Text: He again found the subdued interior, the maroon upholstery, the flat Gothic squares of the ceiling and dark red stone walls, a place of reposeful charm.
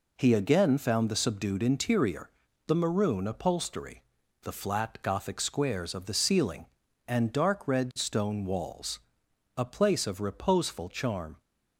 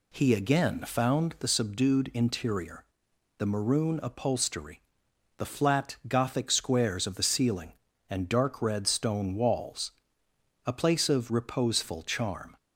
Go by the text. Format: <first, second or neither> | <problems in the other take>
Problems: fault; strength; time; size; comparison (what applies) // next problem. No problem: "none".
neither | none